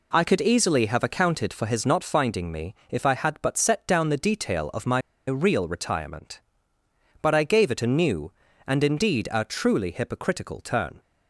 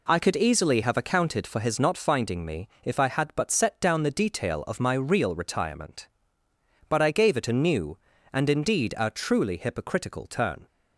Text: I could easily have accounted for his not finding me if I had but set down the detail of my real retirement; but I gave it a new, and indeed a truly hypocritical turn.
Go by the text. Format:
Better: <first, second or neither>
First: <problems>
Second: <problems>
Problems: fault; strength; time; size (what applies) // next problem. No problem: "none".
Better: second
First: pauses between "me" and "if"; slight; at 2.7 s; 0.16 s long // pauses between "my" and "real"; slight; at 4.9 s; 0.27 s long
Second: pauses between "me" and "if"; slight; at 2.6 s; 0.16 s long